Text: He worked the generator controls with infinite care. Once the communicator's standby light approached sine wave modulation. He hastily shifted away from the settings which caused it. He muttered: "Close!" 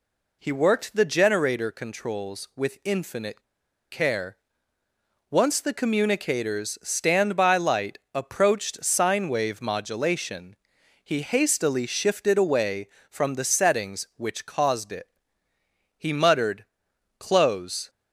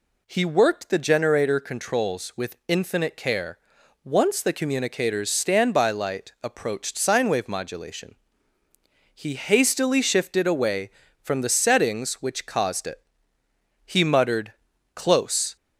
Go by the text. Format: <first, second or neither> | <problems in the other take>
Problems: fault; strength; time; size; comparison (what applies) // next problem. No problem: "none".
second | pauses between "infinite" and "care"; noticeable; at 3.4 s; 0.49 s long